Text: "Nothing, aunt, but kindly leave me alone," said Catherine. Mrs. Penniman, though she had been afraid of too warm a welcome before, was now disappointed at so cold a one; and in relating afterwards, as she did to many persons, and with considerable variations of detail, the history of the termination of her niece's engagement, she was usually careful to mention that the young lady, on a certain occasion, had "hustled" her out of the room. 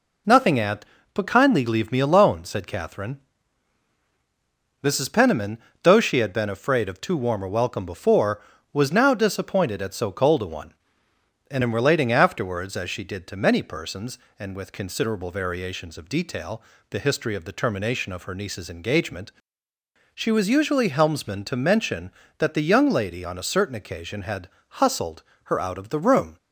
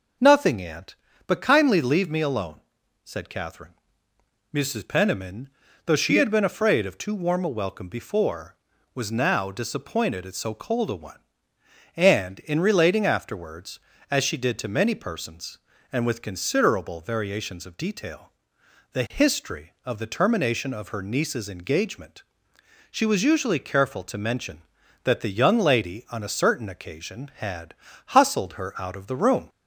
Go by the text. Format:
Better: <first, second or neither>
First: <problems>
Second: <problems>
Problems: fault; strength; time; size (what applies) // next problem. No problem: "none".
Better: second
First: says "helmsman" for "careful"; at 20.8 s // pauses between "had" and "hustled"; slight; at 24.4 s; 0.30 s long // pauses between "hustled" and "her"; slight; at 25.2 s; 0.22 s long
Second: pauses between "had" and "hustled"; slight; at 27.7 s; 0.34 s long